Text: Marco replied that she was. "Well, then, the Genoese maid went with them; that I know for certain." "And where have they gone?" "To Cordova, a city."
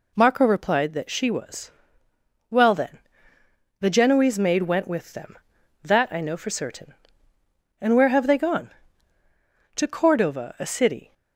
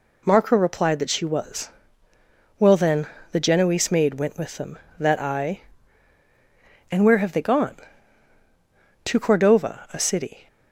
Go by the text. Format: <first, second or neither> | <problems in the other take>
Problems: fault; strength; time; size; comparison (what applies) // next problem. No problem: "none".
first | skips "know for certain"; at 6.2 s